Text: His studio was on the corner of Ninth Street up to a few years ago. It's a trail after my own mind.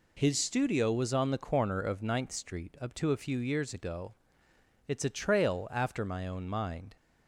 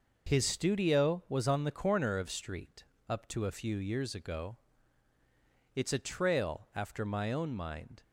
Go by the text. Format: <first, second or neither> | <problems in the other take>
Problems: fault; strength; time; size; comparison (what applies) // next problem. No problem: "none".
first | skips "Ninth"; at 2.2 s // pauses between "Street" and "up"; slight; at 2.8 s; 0.24 s long